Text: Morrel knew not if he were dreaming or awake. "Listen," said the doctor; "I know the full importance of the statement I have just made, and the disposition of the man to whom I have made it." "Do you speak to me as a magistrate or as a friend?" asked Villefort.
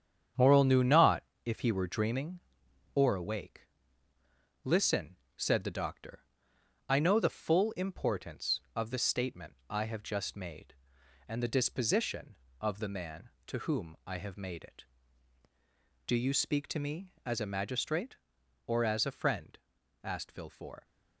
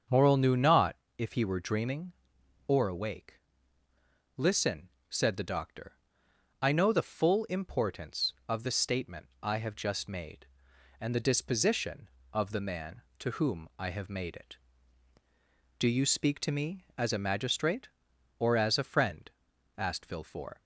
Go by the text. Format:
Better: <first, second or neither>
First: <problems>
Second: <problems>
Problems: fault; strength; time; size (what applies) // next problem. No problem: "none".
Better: second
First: gets quieter; strong; throughout; 8 dB // starts louder than the rest; strong; until 1.6 s; 8 dB // pauses between "not" and "if"; slight; at 1.2 s; 0.24 s long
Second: starts louder than the rest; until 1.3 s; 7 dB // pauses between "not" and "if"; slight; at 0.9 s; 0.24 s long